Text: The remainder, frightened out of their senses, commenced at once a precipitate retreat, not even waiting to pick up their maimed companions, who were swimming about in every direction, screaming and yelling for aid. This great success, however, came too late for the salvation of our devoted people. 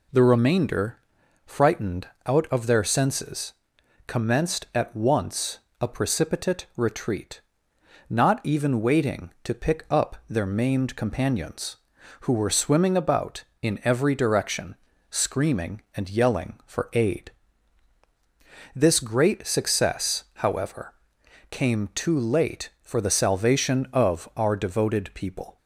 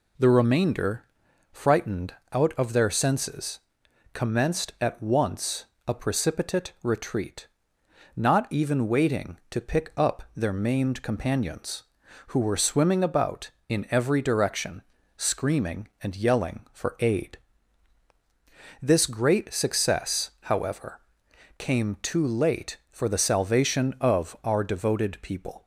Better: neither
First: pauses between "frightened" and "out"; slight; at 2.0 s; 0.18 s long // pauses between "once" and "a"; slight; at 5.5 s; 0.22 s long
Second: pauses between "frightened" and "out"; slight; at 2.1 s; 0.18 s long // pauses between "once" and "a"; slight; at 5.6 s; 0.22 s long

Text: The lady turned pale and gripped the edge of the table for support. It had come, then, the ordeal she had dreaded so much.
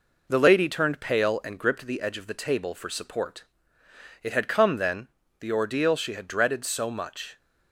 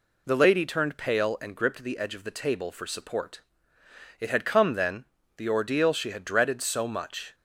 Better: second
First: gets quieter; slight; throughout; 2.5 dB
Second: none

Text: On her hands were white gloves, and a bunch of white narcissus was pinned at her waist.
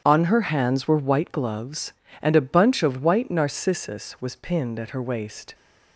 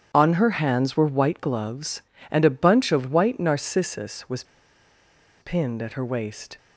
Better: first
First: starts louder than the rest; strong; until 1.0 s; 8.5 dB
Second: starts louder than the rest; strong; until 1.1 s; 8.5 dB // pauses between "was" and "pinned"; noticeable; at 4.4 s; 0.97 s long

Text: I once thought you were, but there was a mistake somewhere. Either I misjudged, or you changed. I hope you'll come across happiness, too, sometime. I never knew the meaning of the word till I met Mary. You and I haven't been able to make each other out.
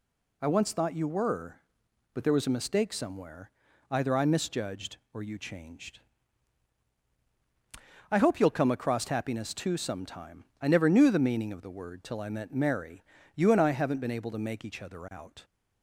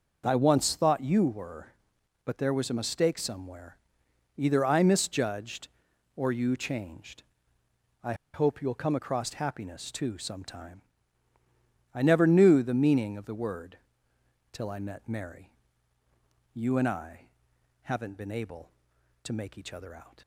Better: first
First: none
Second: pauses between "I" and "hope"; slight; at 8.1 s; 0.19 s long // pauses between "word" and "till"; noticeable; at 13.7 s; 0.74 s long // pauses between "I" and "haven't"; noticeable; at 17.2 s; 0.56 s long

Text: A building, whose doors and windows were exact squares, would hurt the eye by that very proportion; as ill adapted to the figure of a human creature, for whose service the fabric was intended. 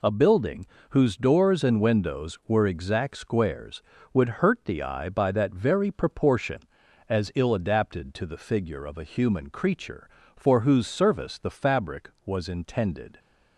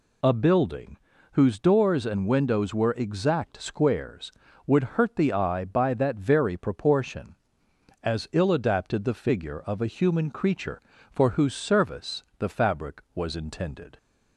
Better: first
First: none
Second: skips "to"; at 9.0 s // pauses between "service" and "the"; slight; at 12.2 s; 0.16 s long

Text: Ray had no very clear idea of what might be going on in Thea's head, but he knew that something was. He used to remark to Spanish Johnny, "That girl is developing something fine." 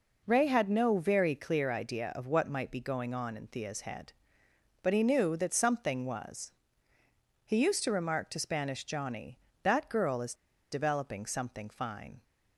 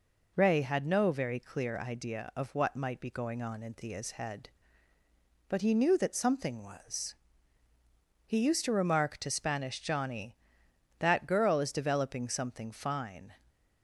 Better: second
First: pauses between "is" and "developing"; at 10.3 s; 0.38 s long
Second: none

